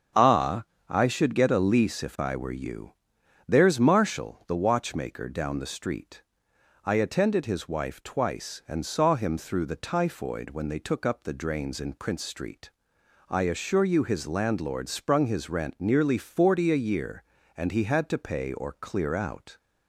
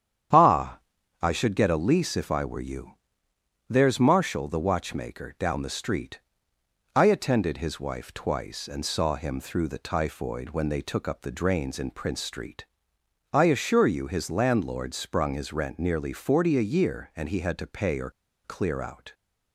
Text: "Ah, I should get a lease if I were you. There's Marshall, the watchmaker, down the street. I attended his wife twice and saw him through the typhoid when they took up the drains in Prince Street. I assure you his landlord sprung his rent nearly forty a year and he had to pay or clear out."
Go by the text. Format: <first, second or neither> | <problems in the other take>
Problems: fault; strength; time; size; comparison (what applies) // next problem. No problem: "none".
first | starts louder than the rest; strong; until 1.7 s; 9 dB; strong in the first // pauses between "or" and "clear"; slight; at 18.0 s; 0.35 s long